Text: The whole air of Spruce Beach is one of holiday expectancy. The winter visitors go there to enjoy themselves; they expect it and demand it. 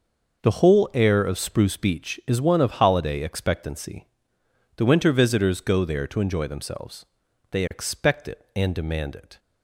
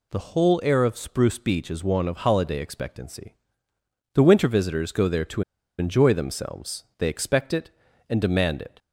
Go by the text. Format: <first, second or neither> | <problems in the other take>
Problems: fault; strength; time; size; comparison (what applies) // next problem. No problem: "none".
first | pauses between "to" and "enjoy"; at 5.4 s; 0.37 s long